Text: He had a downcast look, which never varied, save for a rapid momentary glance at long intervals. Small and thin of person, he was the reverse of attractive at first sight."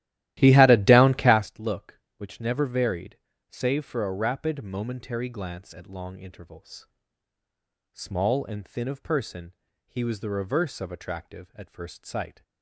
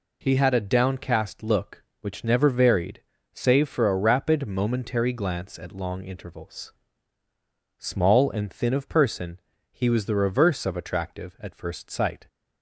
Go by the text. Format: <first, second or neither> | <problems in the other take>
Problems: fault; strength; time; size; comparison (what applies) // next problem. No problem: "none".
second | starts louder than the rest; strong; until 1.6 s; 14.5 dB